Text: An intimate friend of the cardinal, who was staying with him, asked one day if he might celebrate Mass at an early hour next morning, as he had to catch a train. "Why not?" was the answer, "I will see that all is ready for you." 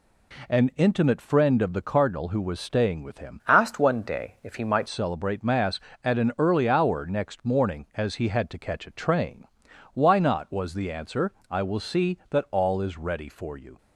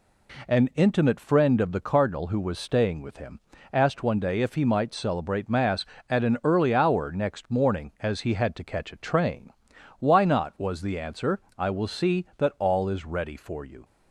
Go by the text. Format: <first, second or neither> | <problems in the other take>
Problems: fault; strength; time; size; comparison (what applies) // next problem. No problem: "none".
second | changes voice from "asked" to "might"; from 3.4 to 4.8 s; 1.4 s long